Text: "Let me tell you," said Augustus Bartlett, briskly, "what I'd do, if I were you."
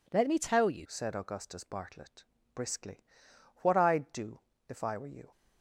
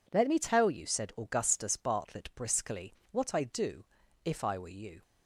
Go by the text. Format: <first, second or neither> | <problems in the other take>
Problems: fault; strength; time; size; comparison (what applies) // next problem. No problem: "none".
second | changes voice at "said"; from 0.8 s on; 4.5 s long